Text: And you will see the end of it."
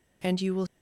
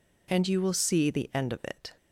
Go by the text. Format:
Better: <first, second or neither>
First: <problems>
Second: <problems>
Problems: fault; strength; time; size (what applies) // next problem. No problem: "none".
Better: second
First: stops before "see the end of it"; at 0.6 s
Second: none